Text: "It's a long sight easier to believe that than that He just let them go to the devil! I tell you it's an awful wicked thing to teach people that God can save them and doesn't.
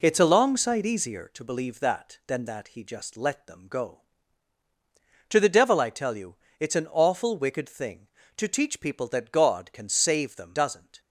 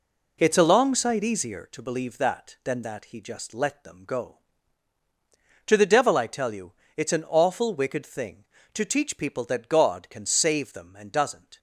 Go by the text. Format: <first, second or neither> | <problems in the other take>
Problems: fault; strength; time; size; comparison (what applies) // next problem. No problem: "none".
second | pauses between "you" and "it's"; slight; at 6.3 s; 0.22 s long; slight in the second // skips "and"; at 10.5 s